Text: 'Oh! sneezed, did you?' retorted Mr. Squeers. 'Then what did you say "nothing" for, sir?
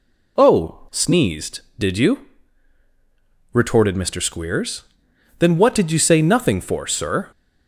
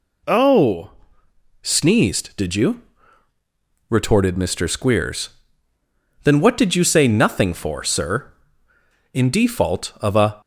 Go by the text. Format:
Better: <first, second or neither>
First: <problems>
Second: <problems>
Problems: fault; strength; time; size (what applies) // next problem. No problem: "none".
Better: first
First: none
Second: goes on to say "In default of a"; noticeable; from 9.1 s on; 1.2 s long